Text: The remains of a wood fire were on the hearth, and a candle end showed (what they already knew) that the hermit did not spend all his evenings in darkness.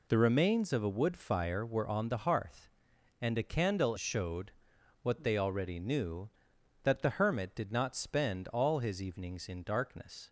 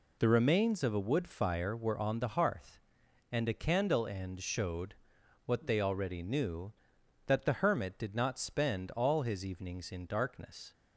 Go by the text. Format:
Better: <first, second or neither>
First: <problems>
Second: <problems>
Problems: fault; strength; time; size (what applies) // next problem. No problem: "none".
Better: second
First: skips "end"; at 3.9 s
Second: none